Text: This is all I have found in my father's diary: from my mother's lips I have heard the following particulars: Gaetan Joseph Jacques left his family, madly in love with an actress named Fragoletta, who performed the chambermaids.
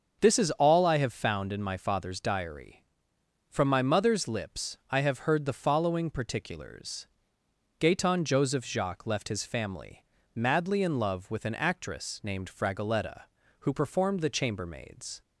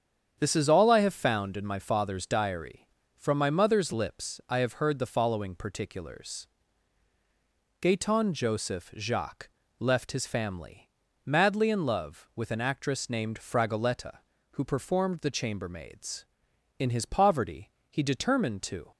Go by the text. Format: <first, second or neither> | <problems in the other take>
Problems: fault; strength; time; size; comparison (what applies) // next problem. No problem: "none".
first | starts louder than the rest; strong; until 1.3 s; 8 dB; also in the first // pauses between "Jacques" and "left"; slight; at 9.4 s; 0.32 s long // goes on to say "In his poverty he determined to"; strong; from 16.7 s on; 2.1 s long